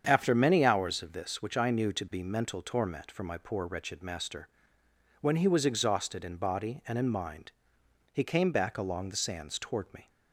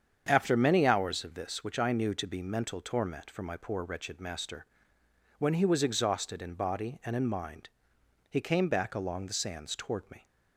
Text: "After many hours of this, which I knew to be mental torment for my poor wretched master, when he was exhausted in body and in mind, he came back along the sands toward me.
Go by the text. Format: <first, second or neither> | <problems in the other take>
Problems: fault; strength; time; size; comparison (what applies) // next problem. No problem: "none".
neither | starts louder than the rest; strong; the same in both